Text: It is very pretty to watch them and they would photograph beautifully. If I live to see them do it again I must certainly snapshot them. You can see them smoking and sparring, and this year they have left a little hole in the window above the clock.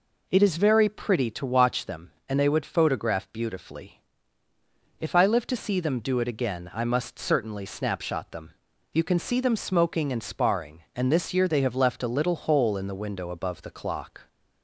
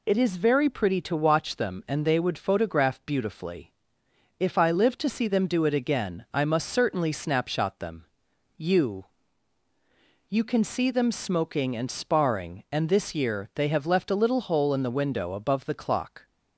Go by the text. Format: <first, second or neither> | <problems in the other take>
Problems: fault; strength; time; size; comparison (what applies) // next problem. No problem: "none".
first | says "You" twice; at 10.2 s